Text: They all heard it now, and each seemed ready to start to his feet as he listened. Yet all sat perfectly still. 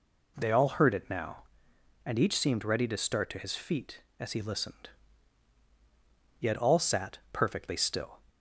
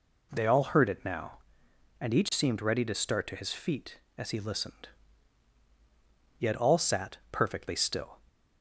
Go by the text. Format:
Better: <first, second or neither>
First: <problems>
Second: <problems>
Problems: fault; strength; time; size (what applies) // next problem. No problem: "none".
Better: neither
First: pauses between "sat" and "perfectly"; slight; at 7.1 s; 0.16 s long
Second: pauses between "sat" and "perfectly"; slight; at 7.1 s; 0.16 s long